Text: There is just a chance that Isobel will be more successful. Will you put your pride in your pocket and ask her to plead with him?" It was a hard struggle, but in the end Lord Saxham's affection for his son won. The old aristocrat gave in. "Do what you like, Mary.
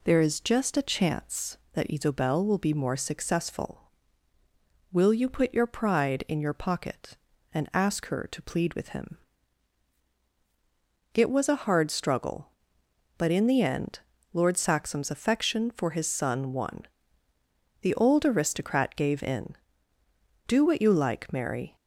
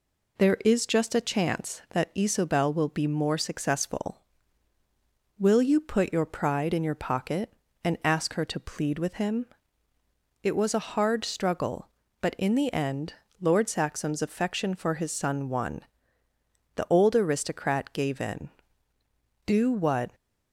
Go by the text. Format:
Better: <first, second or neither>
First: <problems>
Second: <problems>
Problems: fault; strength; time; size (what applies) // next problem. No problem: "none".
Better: first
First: pauses between "end" and "Lord"; slight; at 13.9 s; 0.34 s long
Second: pauses between "end" and "Lord"; slight; at 13.1 s; 0.26 s long // stops before "you like Mary"; at 20.1 s